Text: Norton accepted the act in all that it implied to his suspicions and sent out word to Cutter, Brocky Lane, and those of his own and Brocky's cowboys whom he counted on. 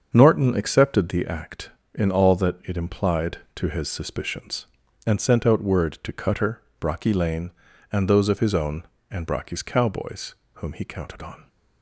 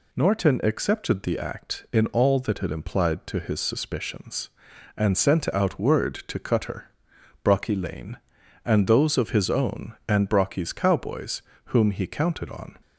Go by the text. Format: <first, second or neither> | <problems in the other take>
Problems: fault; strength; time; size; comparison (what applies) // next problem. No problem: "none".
second | starts louder than the rest; until 1.2 s; 7 dB // pauses between "cowboys" and "whom"; slight; at 10.3 s; 0.20 s long; slight in the second